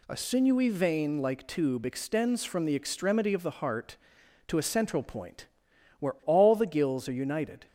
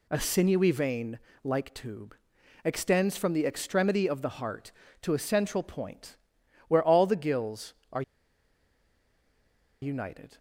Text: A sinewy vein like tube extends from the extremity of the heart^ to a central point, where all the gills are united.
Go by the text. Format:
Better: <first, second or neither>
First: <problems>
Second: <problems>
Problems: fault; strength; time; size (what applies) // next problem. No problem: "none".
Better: first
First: none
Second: pauses between "vein" and "like"; slight; at 1.1 s; 0.26 s long // pauses between "tube" and "extends"; noticeable; at 2.1 s; 0.50 s long // pauses between "are" and "united"; strong; at 8.0 s; 1.8 s long